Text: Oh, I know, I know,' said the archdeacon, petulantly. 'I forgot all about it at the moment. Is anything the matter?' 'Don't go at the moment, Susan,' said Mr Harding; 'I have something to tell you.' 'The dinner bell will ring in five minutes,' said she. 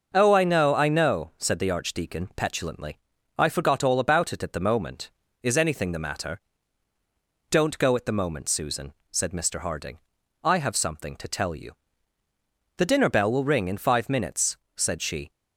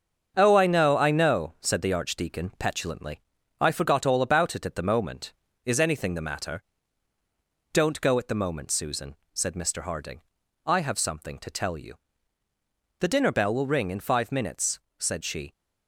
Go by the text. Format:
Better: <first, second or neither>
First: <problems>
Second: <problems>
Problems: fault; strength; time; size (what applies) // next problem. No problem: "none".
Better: first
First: none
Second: gets quieter; noticeable; throughout; 6 dB